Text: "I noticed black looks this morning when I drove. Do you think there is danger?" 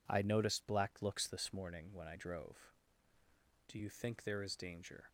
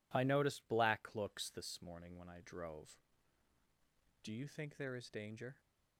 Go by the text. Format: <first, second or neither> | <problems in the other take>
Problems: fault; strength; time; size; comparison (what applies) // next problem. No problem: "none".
neither | none